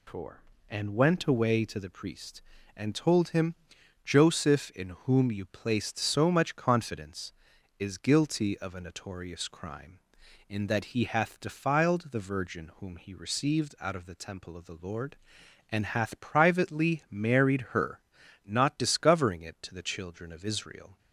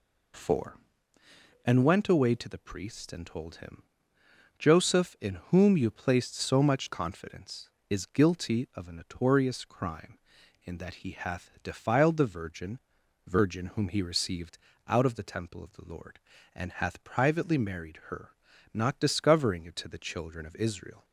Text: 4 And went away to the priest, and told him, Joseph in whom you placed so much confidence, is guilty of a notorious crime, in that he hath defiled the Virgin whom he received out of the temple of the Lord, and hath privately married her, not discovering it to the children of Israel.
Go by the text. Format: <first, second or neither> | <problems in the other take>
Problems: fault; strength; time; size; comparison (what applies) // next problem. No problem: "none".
first | pauses between "in" and "whom"; slight; at 5.3 s; 0.16 s long // says "Virgin" twice; at 13.2 s // pauses between "received" and "out"; slight; at 14.5 s; 0.28 s long